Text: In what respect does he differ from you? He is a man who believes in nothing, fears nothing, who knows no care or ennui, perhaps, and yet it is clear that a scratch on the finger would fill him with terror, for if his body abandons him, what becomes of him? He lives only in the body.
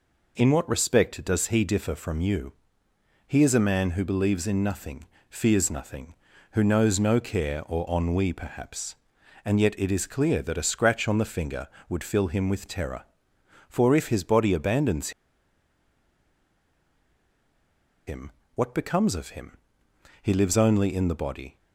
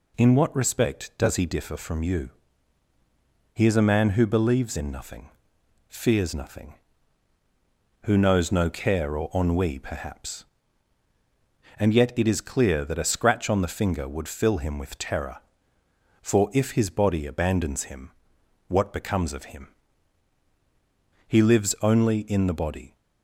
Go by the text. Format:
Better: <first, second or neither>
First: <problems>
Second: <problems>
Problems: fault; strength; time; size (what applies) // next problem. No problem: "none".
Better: second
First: pauses between "abandons" and "him"; strong; at 15.1 s; 2.9 s long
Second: none